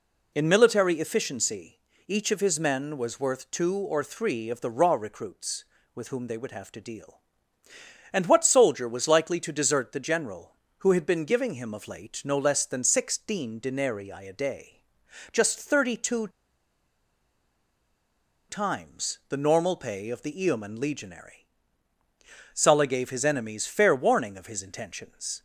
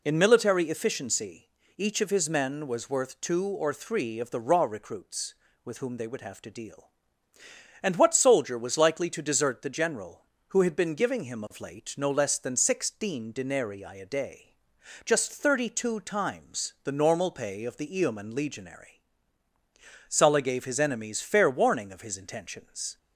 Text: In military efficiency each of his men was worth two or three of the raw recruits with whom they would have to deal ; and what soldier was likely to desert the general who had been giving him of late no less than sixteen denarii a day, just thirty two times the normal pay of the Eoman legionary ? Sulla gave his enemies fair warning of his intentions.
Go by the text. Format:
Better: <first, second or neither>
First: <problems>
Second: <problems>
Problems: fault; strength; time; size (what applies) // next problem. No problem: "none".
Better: second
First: pauses between "efficiency" and "each"; slight; at 1.7 s; 0.28 s long // pauses between "two" and "times"; strong; at 16.2 s; 2.2 s long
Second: pauses between "efficiency" and "each"; slight; at 1.4 s; 0.28 s long